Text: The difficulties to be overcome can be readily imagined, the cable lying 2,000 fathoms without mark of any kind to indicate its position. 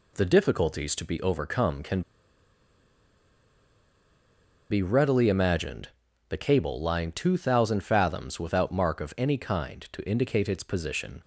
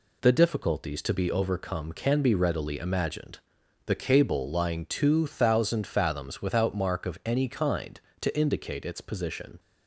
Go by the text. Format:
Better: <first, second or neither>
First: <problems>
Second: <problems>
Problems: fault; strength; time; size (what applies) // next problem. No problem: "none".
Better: second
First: pauses between "can" and "be"; strong; at 2.0 s; 2.6 s long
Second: none